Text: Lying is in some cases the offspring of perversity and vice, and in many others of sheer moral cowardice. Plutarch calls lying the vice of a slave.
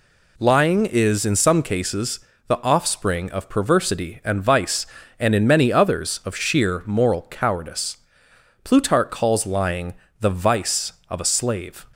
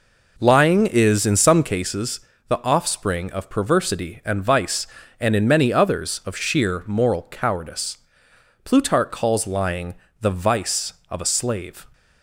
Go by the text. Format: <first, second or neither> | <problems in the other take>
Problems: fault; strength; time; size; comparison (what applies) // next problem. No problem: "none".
first | starts louder than the rest; noticeable; until 1.8 s; 4.5 dB // pauses between "cases" and "the"; slight; at 2.1 s; 0.28 s long; slight in the first // pauses between "lying" and "the"; slight; at 9.9 s; 0.26 s long; slight in the first